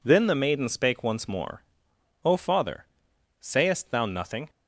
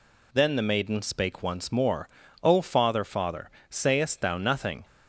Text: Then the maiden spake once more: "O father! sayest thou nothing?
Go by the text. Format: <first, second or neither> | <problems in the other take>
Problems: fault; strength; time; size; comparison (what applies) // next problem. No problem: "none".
first | says "father" twice; at 3.0 s